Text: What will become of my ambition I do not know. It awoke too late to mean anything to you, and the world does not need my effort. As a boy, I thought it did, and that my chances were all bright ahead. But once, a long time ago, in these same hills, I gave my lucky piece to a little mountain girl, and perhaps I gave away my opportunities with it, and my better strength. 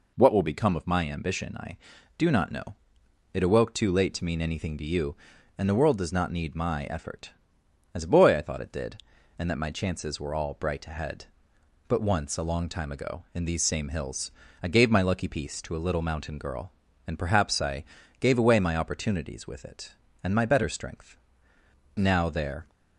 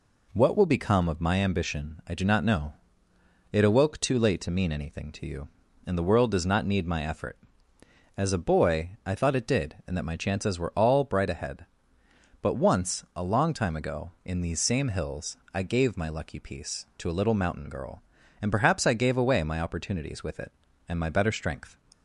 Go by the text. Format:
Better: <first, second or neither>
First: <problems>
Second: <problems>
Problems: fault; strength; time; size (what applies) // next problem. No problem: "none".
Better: second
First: pauses between "I" and "gave"; slight; at 17.8 s; 0.36 s long // goes on to say "Now there"; noticeable; from 21.9 s on; 0.74 s long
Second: none